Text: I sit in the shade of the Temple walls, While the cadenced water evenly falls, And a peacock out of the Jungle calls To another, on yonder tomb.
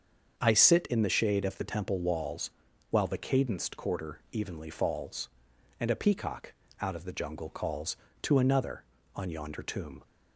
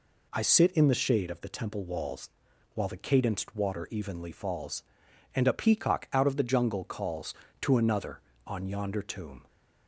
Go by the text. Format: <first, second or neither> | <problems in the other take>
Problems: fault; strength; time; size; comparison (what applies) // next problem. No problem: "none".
second | starts louder than the rest; until 1.4 s; 7 dB // says "quarter" for "water"; at 3.7 s // pauses between "peacock" and "out"; slight; at 6.5 s; 0.26 s long